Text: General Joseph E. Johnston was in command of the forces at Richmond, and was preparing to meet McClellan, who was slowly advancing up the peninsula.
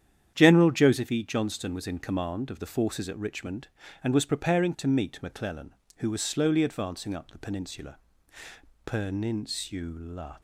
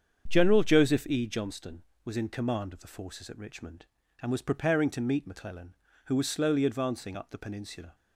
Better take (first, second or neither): second